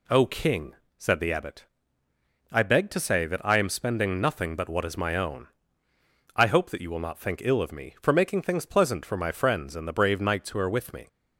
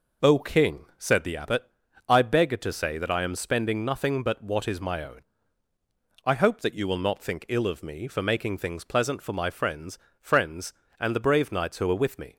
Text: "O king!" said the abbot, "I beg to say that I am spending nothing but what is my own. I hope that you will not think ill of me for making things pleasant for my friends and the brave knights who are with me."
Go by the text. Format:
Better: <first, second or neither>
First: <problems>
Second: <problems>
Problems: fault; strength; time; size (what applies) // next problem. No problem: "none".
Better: first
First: none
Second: says "friends" twice; at 10.2 s